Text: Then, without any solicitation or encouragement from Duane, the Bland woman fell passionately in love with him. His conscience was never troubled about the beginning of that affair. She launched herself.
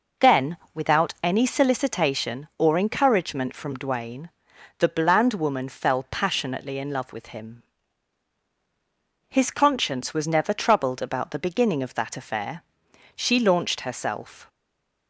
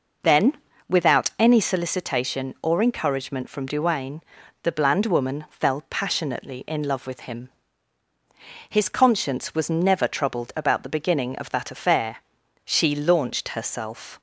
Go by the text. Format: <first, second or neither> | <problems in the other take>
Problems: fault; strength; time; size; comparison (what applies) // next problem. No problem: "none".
second | stays silent after the last word; slight; from 14.4 s on; 0.6 s long